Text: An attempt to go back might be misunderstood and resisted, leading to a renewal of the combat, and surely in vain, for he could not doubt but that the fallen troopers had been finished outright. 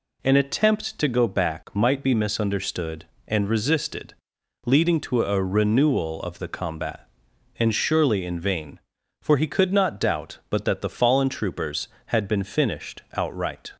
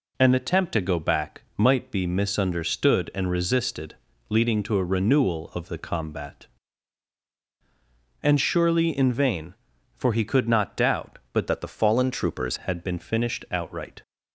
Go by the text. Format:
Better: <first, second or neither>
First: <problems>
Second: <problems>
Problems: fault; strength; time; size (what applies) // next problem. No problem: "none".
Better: first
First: none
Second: changes voice from "that" to "troopers"; from 11.4 to 12.5 s; 1.1 s long